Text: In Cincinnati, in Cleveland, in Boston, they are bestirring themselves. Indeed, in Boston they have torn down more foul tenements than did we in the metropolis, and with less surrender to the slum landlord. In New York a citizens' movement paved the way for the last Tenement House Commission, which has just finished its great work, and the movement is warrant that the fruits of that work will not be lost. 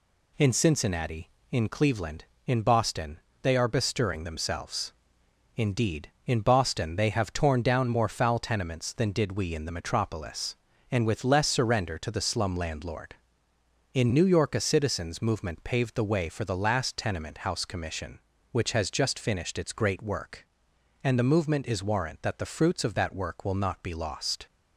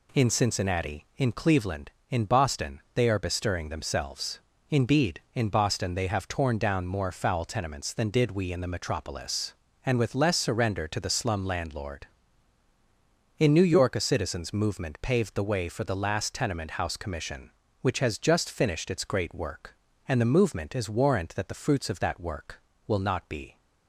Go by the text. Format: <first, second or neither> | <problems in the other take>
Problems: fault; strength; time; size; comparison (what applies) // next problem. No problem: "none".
first | stops before "lost"; at 23.5 s